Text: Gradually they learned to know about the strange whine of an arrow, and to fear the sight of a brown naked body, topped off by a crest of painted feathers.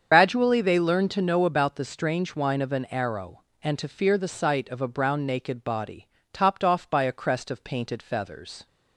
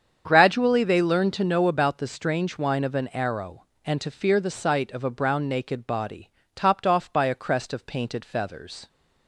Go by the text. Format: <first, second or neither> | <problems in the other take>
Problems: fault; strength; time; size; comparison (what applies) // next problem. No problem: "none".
second | loses the start of "Gradually"; at 0.1 s; 90 ms // starts louder than the rest; strong; until 1.1 s; 7.5 dB; strong in the second